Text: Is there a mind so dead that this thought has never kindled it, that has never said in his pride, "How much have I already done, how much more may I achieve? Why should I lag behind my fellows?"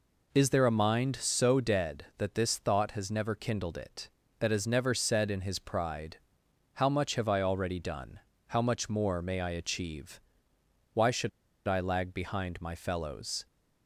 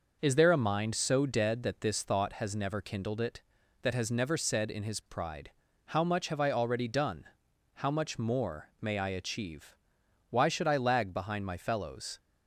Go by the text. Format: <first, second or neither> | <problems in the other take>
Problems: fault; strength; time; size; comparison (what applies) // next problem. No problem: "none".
second | pauses between "should" and "I"; at 11.2 s; 0.38 s long